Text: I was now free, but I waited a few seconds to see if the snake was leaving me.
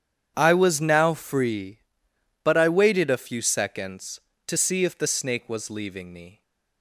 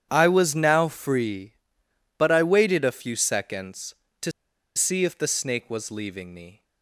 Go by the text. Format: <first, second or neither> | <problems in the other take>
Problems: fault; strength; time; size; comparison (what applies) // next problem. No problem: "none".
first | starts louder than the rest; strong; until 1.1 s; 9 dB; strong in the first // pauses between "to" and "see"; at 4.3 s; 0.45 s long